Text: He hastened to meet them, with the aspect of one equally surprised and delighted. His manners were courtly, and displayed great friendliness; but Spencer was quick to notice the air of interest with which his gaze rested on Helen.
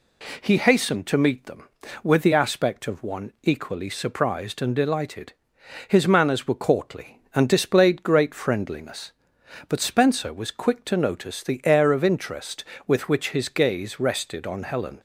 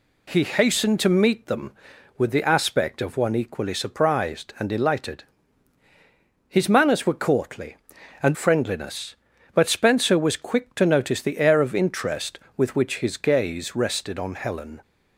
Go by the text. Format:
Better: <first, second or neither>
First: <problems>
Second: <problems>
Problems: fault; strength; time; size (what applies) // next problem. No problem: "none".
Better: first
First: none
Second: skips "displayed great"; at 8.3 s